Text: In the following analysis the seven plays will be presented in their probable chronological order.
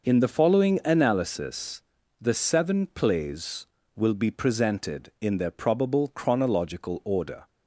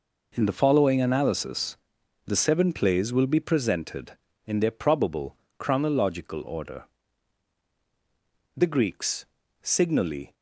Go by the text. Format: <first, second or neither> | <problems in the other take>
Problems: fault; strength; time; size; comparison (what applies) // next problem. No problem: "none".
first | pauses between "analysis" and "the"; noticeable; at 1.7 s; 0.48 s long; also in the first // pauses between "probable" and "chronological"; slight; at 5.3 s; 0.24 s long // goes on to say "The Greeks signally"; strong; from 8.5 s on; 1.7 s long